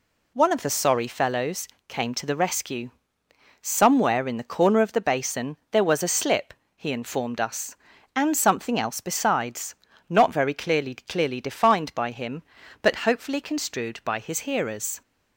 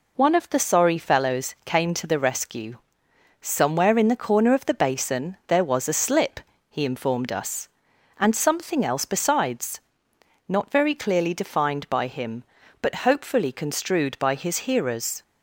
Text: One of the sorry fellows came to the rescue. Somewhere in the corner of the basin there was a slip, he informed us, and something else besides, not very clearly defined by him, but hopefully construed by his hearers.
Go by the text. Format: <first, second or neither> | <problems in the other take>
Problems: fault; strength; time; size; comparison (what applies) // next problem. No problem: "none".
second | pauses between "fellows" and "came"; slight; at 1.6 s; 0.20 s long // says "clearly" twice; at 10.9 s